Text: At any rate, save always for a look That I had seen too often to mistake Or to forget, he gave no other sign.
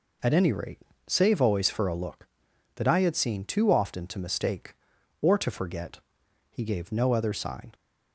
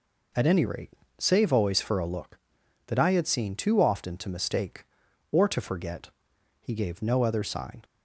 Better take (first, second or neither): neither